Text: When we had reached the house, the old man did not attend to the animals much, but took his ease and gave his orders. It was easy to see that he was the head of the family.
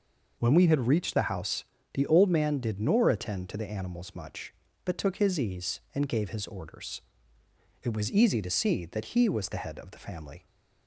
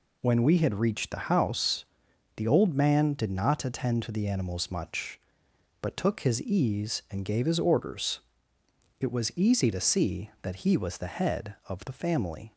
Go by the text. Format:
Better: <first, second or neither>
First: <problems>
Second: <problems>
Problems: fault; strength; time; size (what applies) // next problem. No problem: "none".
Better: second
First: says "nor" for "not"; at 2.7 s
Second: none